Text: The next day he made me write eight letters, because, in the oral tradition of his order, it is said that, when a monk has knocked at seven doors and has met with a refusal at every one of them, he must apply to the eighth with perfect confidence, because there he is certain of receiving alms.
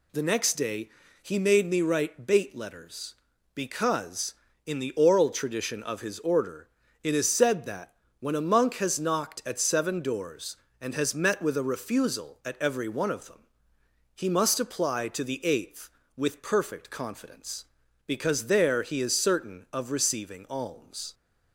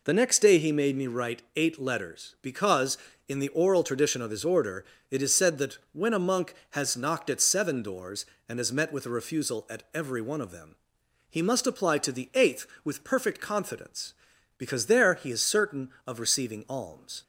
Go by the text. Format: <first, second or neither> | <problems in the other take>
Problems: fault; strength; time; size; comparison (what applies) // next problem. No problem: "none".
second | pauses between "day" and "he"; slight; at 0.8 s; 0.32 s long // says "bait" for "eight"; at 2.2 s